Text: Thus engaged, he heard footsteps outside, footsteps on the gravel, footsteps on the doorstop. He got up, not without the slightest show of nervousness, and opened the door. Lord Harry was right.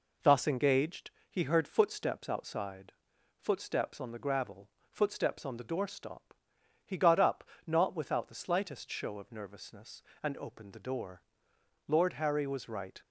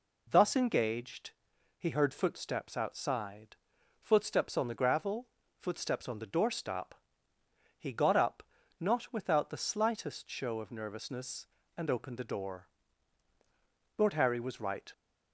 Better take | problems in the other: neither | none

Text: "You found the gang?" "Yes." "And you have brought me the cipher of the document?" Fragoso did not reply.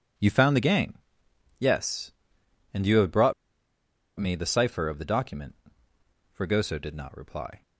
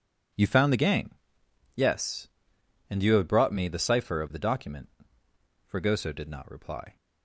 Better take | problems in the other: second | pauses between "brought" and "me"; noticeable; at 3.3 s; 0.86 s long

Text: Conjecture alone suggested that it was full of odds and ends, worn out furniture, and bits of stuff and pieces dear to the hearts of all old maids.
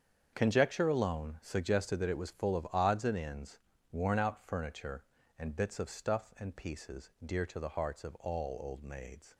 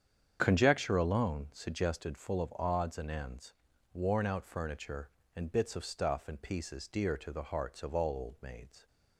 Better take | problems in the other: first | starts louder than the rest; strong; until 1.4 s; 8 dB; strong in the first // skips "that it was"; at 2.1 s

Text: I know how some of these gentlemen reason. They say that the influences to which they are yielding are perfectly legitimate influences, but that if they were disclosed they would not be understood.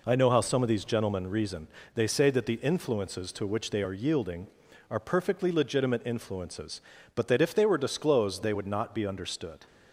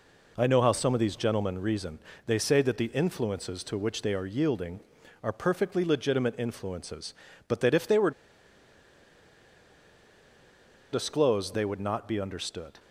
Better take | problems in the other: first | pauses between "were" and "disclosed"; strong; at 8.1 s; 2.8 s long

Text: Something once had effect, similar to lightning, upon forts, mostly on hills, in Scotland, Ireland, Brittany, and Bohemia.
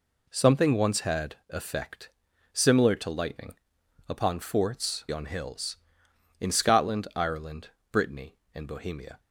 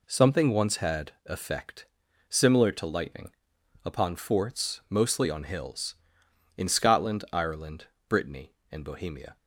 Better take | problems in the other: second | skips "mostly"; at 5.0 s

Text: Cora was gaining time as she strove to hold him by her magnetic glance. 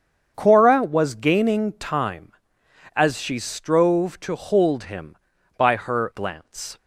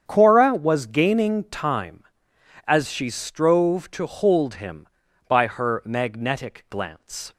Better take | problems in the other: second | starts louder than the rest; strong; until 1.3 s; 7.5 dB; strong in the second // skips "magnetic"; at 6.1 s

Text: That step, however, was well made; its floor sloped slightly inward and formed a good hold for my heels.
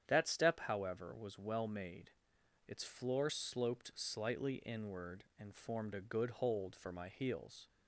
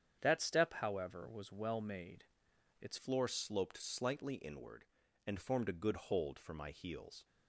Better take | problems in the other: first | starts louder than the rest; strong; until 1.2 s; 8.5 dB; strong in the first // changes voice at "floor"; from 2.9 s on; 4.3 s long

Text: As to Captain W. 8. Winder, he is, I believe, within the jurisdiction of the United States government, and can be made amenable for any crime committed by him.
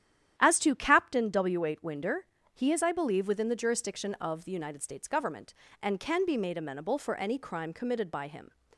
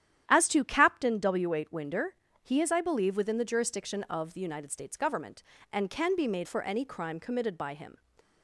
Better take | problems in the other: first | starts louder than the rest; strong; until 1.2 s; 10.5 dB; strong in the first // skips "amenable"; at 6.4 s

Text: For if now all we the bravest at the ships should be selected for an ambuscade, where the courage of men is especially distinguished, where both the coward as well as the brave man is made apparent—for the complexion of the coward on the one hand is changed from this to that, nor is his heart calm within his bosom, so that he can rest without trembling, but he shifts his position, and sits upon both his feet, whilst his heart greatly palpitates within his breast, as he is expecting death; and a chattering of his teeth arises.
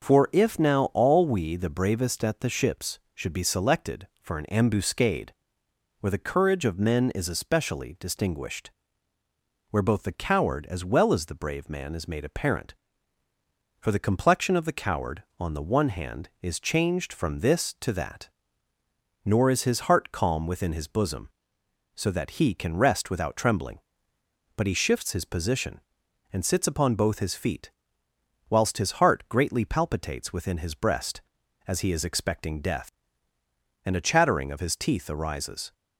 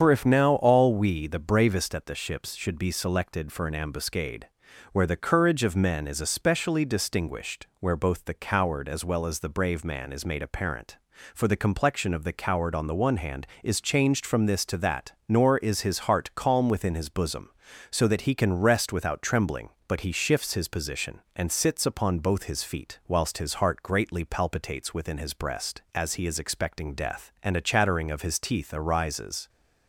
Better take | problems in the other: first | loses the start of "For"; at 0.0 s; 50 ms // starts louder than the rest; strong; until 1.0 s; 7 dB; also in the first

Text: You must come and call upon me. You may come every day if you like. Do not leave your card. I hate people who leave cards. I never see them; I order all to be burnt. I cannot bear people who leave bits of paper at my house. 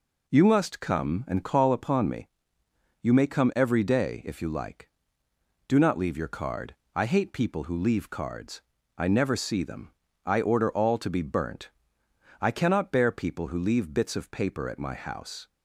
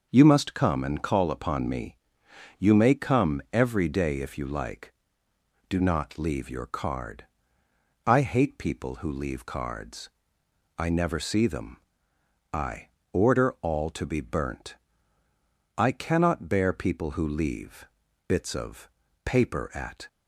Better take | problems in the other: first | pauses between "I" and "order"; slight; at 12.8 s; 0.24 s long // pauses between "leave" and "bits"; at 17.8 s; 0.40 s long // pauses between "of" and "paper"; slight; at 18.8 s; 0.36 s long // stops before "my house"; at 20.0 s

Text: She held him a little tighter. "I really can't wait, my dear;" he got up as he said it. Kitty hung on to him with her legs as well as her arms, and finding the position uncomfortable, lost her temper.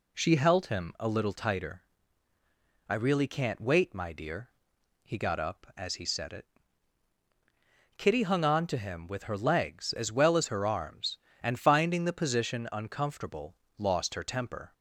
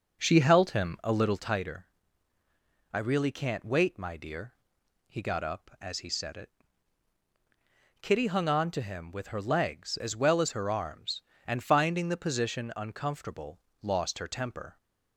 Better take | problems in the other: first | starts louder than the rest; until 1.6 s; 6 dB

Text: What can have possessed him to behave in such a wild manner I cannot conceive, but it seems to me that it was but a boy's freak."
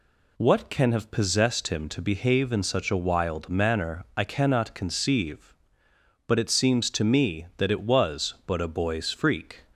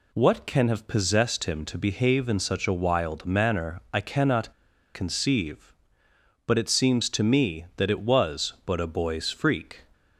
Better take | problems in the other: first | pauses between "cannot" and "conceive"; at 4.5 s; 0.43 s long

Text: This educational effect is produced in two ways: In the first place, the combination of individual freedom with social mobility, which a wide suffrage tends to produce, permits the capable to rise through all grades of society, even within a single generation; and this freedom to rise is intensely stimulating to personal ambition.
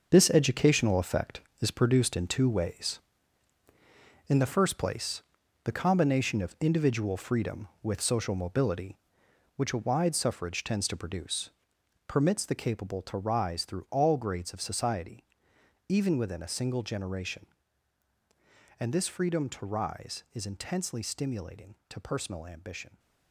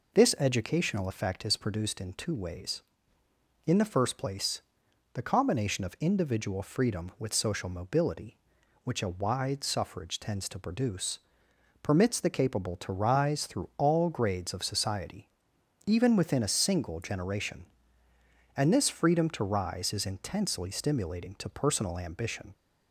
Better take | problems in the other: second | gets quieter; strong; throughout; 10 dB

